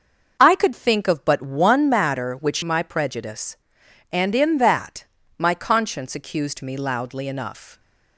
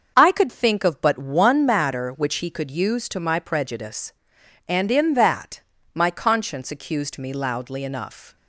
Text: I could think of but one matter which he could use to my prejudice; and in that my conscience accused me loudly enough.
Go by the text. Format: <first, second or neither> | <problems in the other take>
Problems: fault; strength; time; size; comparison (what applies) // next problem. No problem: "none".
second | starts louder than the rest; until 1.4 s; 6 dB; also in the second // skips "he could use to"; at 2.6 s // pauses between "that" and "my"; slight; at 5.0 s; 0.32 s long; slight in the second